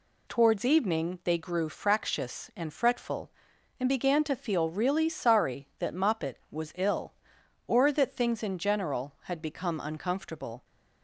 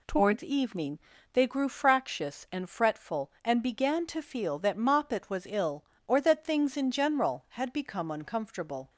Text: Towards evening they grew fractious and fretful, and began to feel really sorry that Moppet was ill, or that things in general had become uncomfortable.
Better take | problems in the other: first | pauses between "evening" and "they"; slight; at 0.9 s; 0.32 s long // skips "really sorry"; at 4.5 s

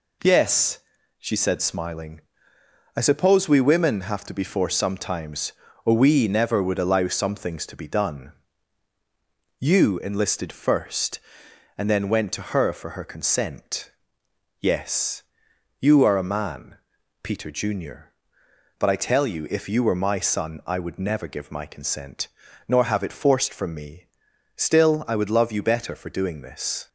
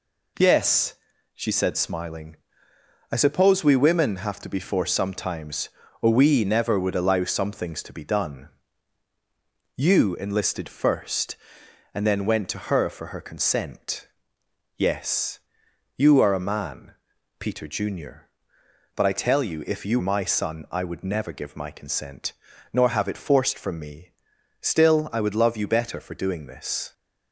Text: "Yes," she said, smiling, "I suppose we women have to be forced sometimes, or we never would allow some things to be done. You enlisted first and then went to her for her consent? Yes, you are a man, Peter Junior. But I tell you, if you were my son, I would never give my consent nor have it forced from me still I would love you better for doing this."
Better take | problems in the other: first | skips "were"; at 20.0 s // pauses between "consent" and "nor"; at 22.3 s; 0.40 s long; also in the first // pauses between "me" and "still"; noticeable; at 24.1 s; 0.50 s long; noticeable in the first

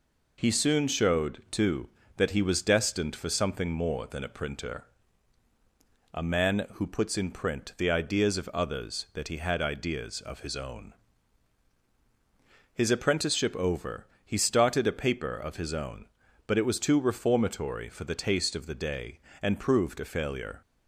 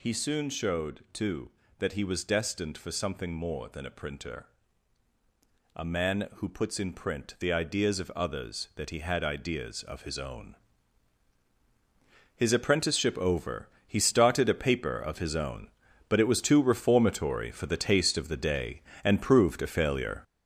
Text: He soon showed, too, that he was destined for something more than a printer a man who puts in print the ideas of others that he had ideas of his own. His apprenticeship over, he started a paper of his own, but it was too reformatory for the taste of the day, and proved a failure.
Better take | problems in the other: first | gets louder; throughout; 7 dB // pauses between "printer" and "a"; strong; at 4.4 s; 1.2 s long; strong in the first

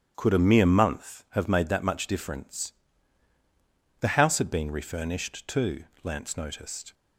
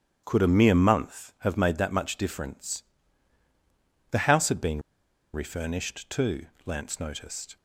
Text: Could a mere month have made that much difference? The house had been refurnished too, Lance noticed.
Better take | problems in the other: first | starts louder than the rest; strong; until 1.2 s; 9.5 dB; strong in the first // pauses between "been" and "refurnished"; noticeable; at 4.8 s; 0.53 s long

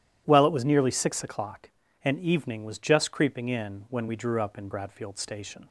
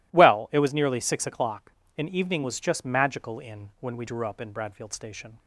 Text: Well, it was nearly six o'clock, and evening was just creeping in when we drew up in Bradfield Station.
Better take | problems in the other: first | says "magical" for "creeping"; at 2.8 s

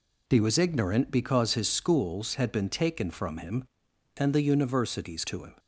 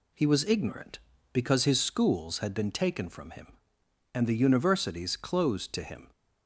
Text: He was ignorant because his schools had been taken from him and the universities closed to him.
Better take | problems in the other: second | skips "closed"; at 5.2 s

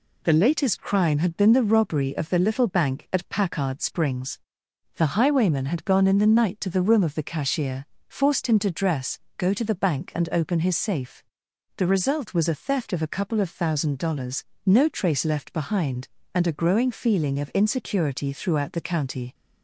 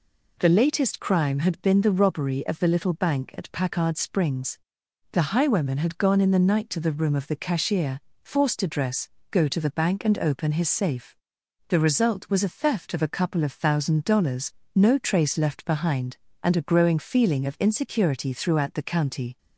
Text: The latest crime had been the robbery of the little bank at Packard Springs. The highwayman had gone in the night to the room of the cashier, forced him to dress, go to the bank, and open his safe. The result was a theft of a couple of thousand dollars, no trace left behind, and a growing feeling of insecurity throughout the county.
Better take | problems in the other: first | skips "him"; at 8.5 s

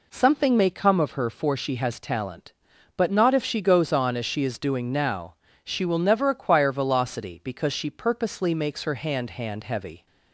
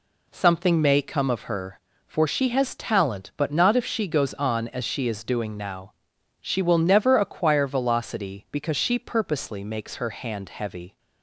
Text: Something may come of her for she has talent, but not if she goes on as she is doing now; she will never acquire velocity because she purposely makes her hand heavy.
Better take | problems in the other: second | says "hand" twice; at 9.3 s

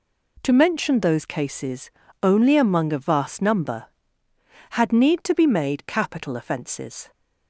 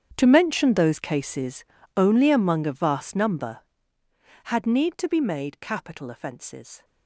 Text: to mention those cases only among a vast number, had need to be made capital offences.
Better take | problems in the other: first | gets quieter; strong; throughout; 19.5 dB // pauses between "cases" and "only"; slight; at 1.6 s; 0.32 s long; slight in the first

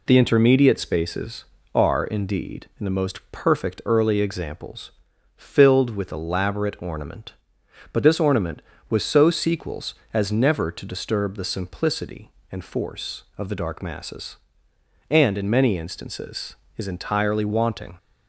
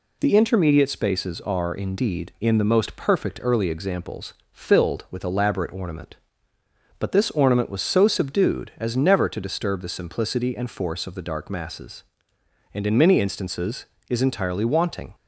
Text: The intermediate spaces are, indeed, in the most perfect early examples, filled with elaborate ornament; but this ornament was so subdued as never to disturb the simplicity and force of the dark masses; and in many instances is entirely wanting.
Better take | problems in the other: second | says "sequels" for "subdued"; at 9.2 s

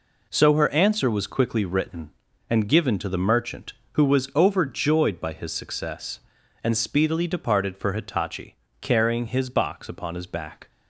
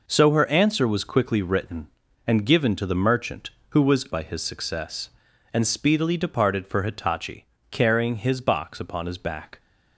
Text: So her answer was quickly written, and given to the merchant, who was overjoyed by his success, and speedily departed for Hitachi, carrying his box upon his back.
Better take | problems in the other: first | skips "overjoyed"; at 4.0 s

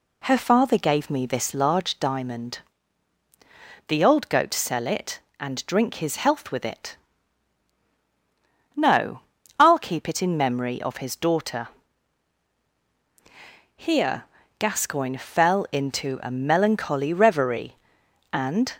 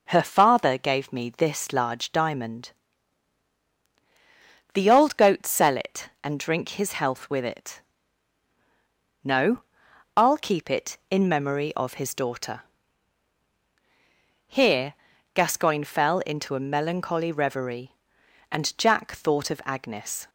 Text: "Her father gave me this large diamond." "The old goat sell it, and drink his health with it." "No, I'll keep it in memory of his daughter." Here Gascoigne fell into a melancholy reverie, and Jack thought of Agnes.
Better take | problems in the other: second | pauses between "Here" and "Gascoigne"; at 14.2 s; 0.38 s long; also in the second // stops before "Jack thought of Agnes"; at 18.7 s

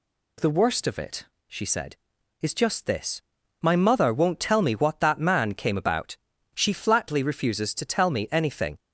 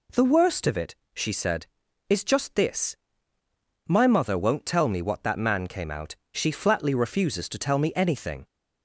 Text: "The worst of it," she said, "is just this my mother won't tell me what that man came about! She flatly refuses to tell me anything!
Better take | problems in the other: first | pauses between "this" and "my"; noticeable; at 2.9 s; 0.90 s long; also in the first // says "out" for "about"; at 5.8 s

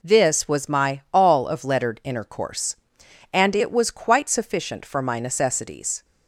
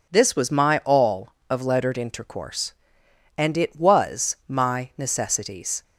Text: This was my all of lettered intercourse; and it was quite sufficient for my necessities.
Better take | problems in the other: first | skips "quite sufficient for"; at 4.4 s

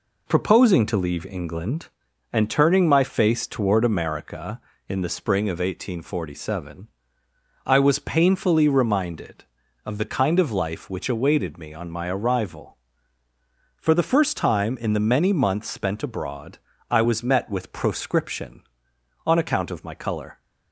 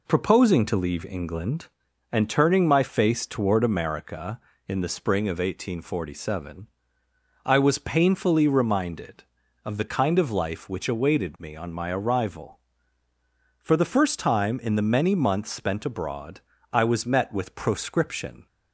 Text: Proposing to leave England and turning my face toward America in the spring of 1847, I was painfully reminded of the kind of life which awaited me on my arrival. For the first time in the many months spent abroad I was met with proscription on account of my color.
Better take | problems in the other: first | pauses between "abroad" and "I"; slight; at 16.4 s; 0.32 s long; slight in the first // stops before "on account of my color"; at 18.4 s

